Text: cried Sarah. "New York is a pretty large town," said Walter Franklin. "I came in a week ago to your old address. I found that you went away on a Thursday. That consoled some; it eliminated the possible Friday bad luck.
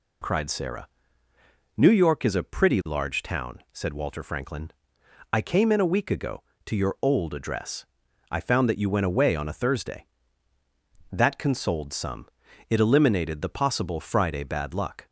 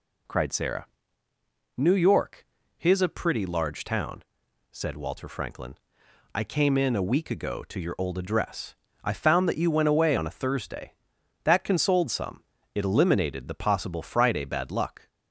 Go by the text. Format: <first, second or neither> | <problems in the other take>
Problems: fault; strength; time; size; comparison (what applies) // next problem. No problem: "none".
first | says "his" for "is"; at 2.7 s